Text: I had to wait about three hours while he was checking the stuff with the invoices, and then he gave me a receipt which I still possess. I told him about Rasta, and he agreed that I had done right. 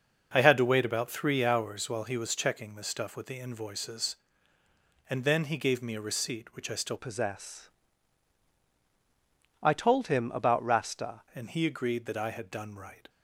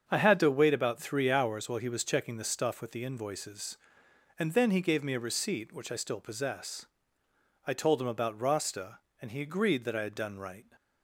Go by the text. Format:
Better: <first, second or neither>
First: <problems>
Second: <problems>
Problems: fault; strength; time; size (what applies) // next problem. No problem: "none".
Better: second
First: starts louder than the rest; noticeable; until 1.3 s; 6 dB // changes voice from "possess" to "Rasta"; from 6.9 to 11.2 s; 4.3 s long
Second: starts louder than the rest; strong; until 1.0 s; 7 dB